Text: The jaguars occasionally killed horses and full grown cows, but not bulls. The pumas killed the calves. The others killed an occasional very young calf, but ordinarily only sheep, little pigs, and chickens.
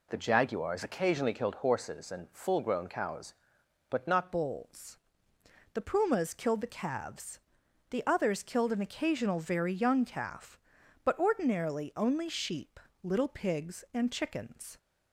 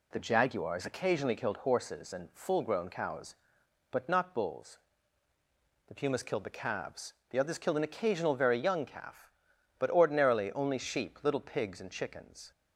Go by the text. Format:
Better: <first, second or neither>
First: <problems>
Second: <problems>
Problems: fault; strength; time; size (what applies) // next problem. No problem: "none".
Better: second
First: changes voice at "bulls"; from 4.3 s on; 10.4 s long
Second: none